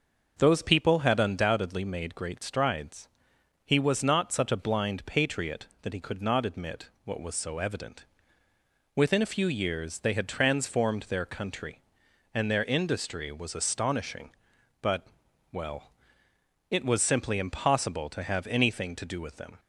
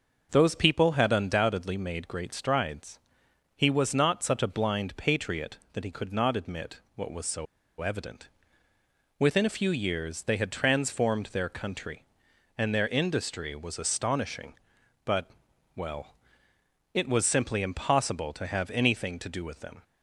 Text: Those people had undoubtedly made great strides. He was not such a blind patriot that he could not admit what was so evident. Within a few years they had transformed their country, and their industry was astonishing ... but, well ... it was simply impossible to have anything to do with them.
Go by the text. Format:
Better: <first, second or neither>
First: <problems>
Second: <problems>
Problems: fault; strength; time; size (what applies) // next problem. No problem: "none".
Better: first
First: starts louder than the rest; until 1.3 s; 6 dB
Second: starts louder than the rest; until 1.3 s; 6 dB // pauses between "so" and "evident"; slight; at 7.4 s; 0.35 s long